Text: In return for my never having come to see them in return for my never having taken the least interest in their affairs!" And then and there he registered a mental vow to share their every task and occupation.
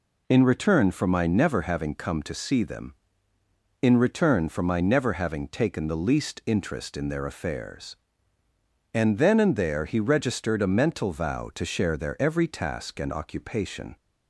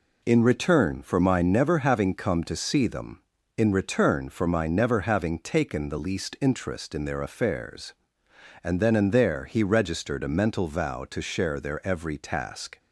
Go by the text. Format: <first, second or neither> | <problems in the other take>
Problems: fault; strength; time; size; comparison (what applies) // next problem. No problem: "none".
first | stops before "and occupation"; at 12.7 s